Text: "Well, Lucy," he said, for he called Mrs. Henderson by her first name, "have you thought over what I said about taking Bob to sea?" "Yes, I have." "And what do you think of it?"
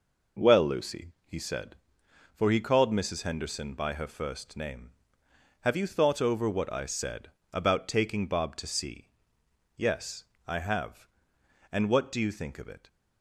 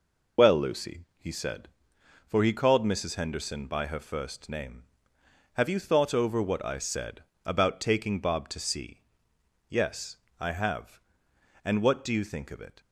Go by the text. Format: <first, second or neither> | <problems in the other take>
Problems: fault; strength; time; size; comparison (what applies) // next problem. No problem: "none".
first | loses the start of "Well"; at 0.3 s; 95 ms // pauses between "said" and "about"; slight; at 7.2 s; 0.20 s long; slight in the first